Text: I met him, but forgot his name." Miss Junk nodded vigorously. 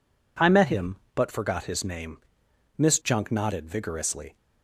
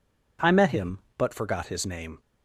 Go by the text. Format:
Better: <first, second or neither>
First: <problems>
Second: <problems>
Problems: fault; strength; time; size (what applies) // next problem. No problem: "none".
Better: first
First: none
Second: stops before "Miss Junk nodded vigorously"; at 2.2 s